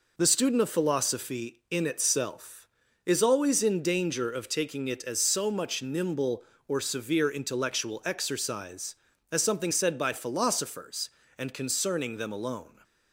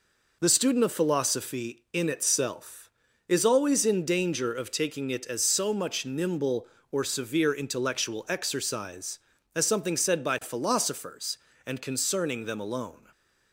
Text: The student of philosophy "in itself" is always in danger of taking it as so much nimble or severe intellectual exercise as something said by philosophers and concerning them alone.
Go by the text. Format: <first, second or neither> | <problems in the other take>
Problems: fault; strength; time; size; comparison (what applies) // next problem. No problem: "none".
neither | none